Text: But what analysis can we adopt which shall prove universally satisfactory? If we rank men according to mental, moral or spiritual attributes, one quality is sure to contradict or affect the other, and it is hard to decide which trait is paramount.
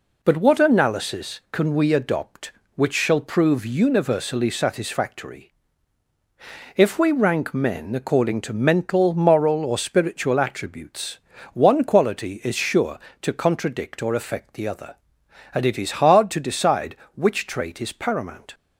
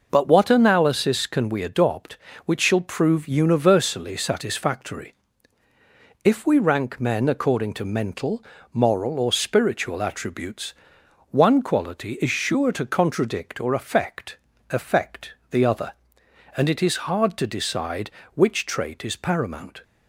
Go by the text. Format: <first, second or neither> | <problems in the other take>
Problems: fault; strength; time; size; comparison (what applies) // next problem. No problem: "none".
first | says "affect" twice; at 14.7 s